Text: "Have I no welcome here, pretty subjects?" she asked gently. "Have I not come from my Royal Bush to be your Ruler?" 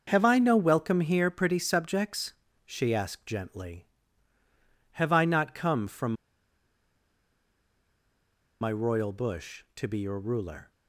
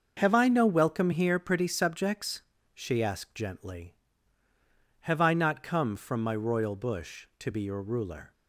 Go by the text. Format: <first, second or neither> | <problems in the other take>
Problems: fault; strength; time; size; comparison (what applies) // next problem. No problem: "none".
second | starts louder than the rest; until 1.0 s; 6.5 dB; also in the second // pauses between "from" and "my"; strong; at 6.1 s; 2.4 s long